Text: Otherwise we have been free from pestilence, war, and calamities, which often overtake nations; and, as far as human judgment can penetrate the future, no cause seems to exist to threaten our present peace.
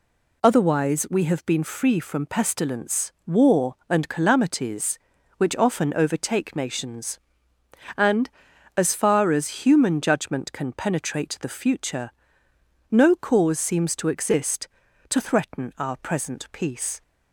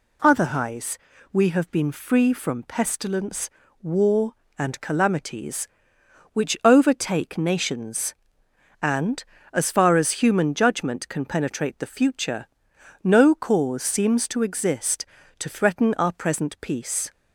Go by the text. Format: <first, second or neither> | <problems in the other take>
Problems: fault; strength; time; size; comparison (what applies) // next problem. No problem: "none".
first | pauses between "Otherwise" and "we"; slight; at 0.9 s; 0.34 s long // skips "often"; at 6.5 s